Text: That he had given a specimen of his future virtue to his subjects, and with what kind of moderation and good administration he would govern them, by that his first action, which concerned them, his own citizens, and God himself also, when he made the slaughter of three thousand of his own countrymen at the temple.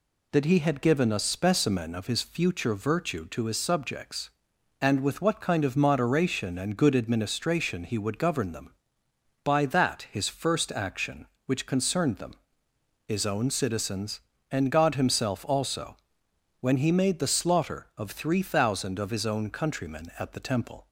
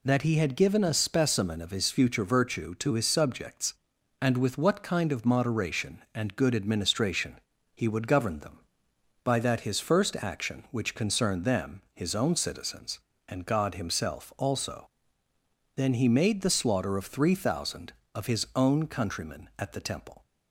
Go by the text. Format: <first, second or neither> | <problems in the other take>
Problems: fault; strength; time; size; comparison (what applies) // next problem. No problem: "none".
first | pauses between "administration" and "he"; slight; at 7.3 s; 0.36 s long // says "then" for "when"; at 15.7 s